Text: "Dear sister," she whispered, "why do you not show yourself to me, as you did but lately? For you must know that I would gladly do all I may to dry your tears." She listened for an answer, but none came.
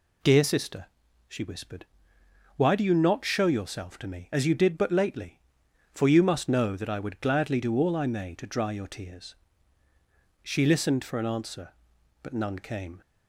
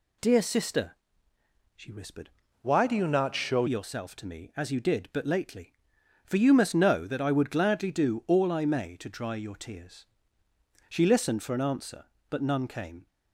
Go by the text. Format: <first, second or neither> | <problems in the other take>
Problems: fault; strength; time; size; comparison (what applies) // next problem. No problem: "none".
first | changes voice from "why" to "show"; from 2.6 to 3.6 s; 1.0 s long